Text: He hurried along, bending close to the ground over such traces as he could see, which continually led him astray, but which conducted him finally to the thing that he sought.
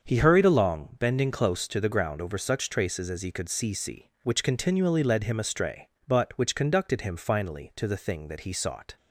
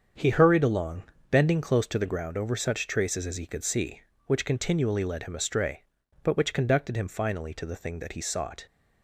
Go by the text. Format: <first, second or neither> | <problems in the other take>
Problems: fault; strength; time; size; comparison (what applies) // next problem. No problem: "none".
second | starts louder than the rest; until 1.0 s; 6.5 dB; strong in the second // says "see" twice; at 3.7 s